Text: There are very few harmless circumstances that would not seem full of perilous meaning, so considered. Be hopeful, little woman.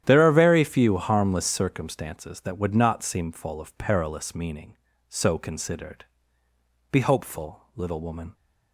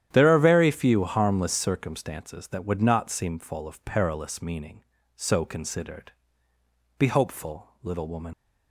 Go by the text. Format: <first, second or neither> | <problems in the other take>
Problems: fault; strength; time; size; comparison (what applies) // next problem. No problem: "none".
first | starts louder than the rest; strong; until 1.1 s; 10.5 dB; strong in the first // leaves "woman" unfinished; at 8.3 s; 70 ms